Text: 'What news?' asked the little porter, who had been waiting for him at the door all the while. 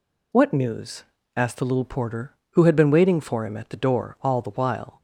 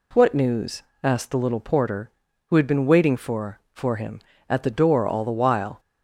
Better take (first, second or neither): first